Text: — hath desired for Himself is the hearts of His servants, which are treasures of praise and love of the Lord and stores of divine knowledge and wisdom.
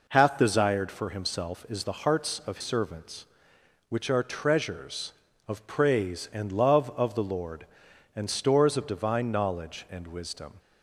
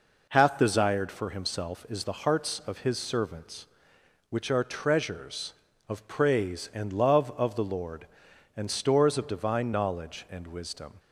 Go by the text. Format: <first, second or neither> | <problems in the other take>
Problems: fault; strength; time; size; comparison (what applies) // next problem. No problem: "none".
second | skips "His"; at 2.5 s